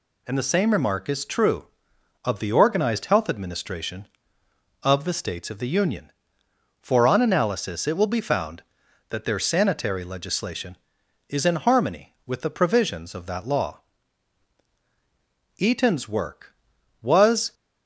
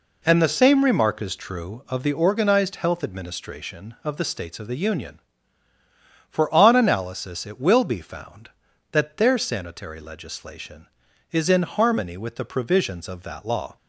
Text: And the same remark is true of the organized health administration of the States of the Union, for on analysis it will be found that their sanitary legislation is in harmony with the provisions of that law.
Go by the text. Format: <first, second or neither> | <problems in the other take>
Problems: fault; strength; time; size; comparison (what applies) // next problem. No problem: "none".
second | goes on to say "Eaton's work was"; strong; from 15.5 s on; 1.9 s long